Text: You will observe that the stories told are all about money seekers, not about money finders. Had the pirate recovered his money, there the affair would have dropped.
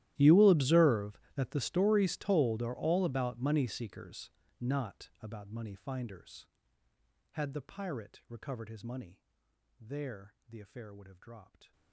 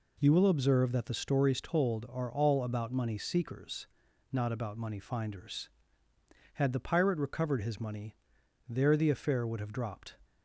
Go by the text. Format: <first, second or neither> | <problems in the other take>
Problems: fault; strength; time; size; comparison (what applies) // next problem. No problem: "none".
second | gets quieter; strong; throughout; 25 dB